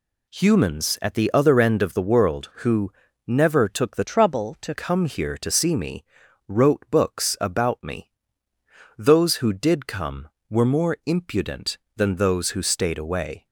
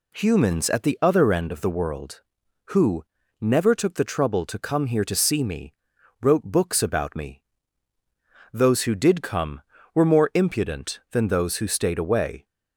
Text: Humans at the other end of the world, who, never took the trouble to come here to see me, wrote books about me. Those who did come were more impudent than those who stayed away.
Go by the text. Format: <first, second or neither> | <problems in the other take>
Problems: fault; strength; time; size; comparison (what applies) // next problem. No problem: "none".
second | changes voice from "trouble" to "to"; from 4.0 to 4.7 s; 0.7 s long